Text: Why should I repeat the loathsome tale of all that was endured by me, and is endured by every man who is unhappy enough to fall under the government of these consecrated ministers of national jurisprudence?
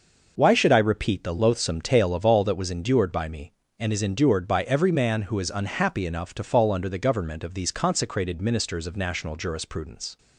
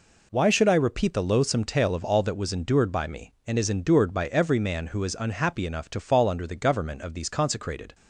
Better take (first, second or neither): first